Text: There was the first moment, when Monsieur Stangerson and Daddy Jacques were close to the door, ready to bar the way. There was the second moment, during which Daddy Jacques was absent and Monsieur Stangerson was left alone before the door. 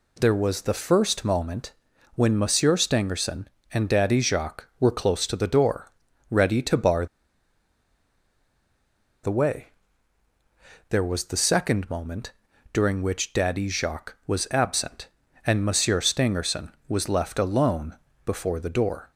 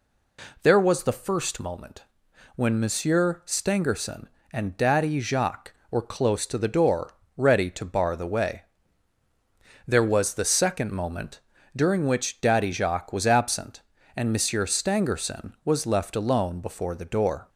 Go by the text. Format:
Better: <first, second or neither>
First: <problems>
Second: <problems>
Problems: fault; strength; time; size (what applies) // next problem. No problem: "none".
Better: second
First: pauses between "bar" and "the"; strong; at 7.0 s; 2.1 s long // pauses between "alone" and "before"; slight; at 17.9 s; 0.28 s long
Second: none